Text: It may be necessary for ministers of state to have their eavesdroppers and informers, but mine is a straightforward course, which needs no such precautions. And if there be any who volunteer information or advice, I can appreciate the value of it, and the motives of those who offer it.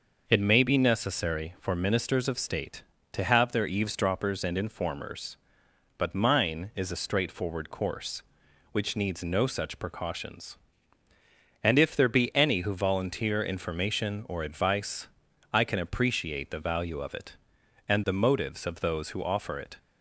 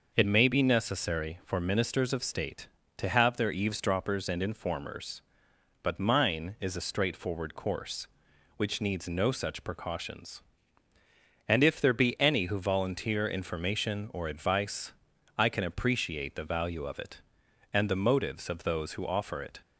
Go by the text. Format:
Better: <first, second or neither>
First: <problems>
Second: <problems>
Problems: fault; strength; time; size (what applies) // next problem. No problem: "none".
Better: neither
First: none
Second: none